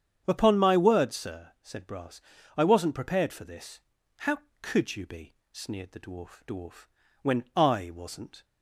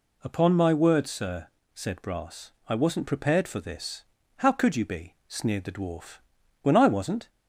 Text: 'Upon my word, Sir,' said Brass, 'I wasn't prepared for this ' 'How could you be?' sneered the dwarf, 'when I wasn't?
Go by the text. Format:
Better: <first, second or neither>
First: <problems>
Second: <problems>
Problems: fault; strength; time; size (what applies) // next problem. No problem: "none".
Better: second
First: starts louder than the rest; strong; until 1.2 s; 8.5 dB // says "dwarf" twice; at 6.4 s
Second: none